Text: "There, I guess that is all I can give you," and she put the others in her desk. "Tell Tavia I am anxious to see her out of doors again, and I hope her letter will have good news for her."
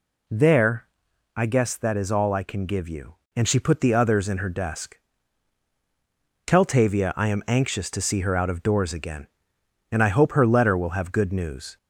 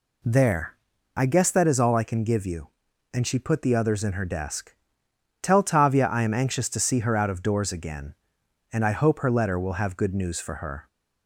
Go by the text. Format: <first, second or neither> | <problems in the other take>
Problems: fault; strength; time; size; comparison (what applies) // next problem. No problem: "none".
second | stops before "for her"; at 11.7 s